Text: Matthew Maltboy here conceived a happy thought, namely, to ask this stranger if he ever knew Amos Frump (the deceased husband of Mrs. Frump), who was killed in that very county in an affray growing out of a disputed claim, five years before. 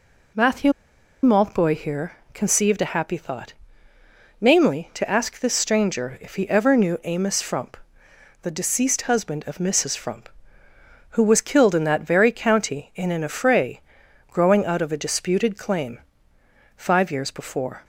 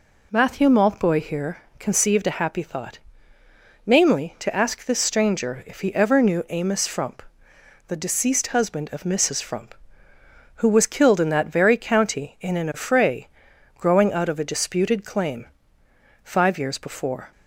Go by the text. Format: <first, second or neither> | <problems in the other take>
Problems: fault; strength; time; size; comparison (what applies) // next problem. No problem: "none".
second | pauses between "Matthew" and "Maltboy"; noticeable; at 0.7 s; 0.51 s long // pauses between "here" and "conceived"; slight; at 2.1 s; 0.22 s long; slight in the second // pauses between "affray" and "growing"; noticeable; at 13.7 s; 0.50 s long; noticeable in the second